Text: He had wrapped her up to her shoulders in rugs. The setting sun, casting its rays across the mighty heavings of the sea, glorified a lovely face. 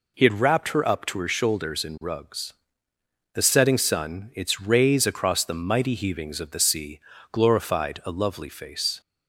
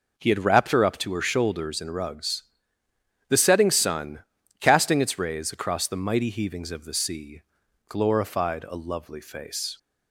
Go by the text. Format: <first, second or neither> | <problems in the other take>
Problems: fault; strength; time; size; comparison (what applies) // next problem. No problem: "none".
second | skips "casting"; at 4.3 s